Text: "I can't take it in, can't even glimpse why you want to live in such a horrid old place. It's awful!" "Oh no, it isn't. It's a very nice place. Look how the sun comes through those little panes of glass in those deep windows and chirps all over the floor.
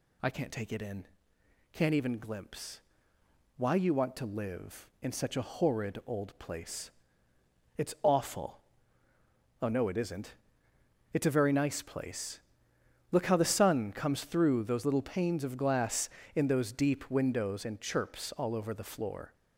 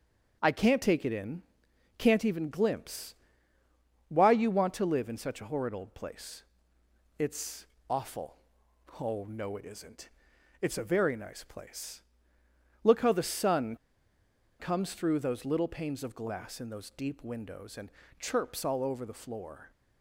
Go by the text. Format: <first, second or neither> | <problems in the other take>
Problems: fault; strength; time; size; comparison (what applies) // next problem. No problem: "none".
first | starts louder than the rest; until 1.4 s; 7 dB // pauses between "glimpse" and "why"; noticeable; at 3.1 s; 0.92 s long; noticeable in the first // pauses between "It's" and "awful"; slight; at 7.6 s; 0.24 s long // pauses between "sun" and "comes"; noticeable; at 13.7 s; 0.84 s long // pauses between "and" and "chirps"; slight; at 17.9 s; 0.28 s long